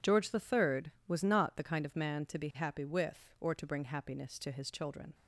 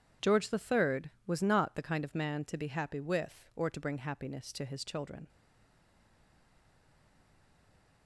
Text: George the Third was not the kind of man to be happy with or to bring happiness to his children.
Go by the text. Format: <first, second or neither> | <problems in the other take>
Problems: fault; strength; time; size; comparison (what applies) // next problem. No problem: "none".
first | stays silent after the last word; strong; from 5.2 s on; 2.8 s long